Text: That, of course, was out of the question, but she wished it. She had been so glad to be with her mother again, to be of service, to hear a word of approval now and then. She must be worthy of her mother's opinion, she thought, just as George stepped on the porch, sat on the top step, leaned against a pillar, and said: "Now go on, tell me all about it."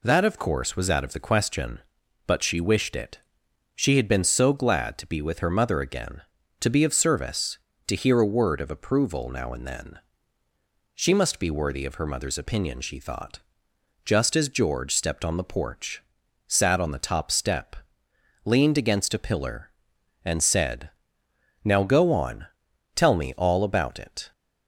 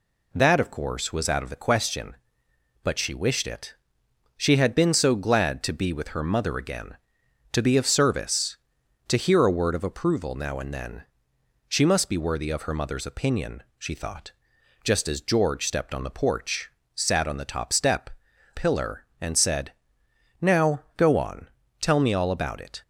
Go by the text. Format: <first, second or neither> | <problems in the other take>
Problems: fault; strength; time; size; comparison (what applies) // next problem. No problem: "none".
first | skips "leaned against a"; at 18.3 s